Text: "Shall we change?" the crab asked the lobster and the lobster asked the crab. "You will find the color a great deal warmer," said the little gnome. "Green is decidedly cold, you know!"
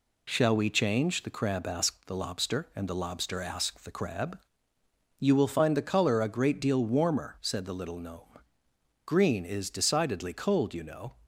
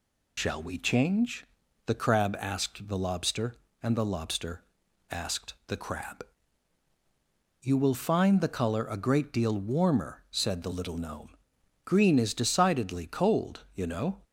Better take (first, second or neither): first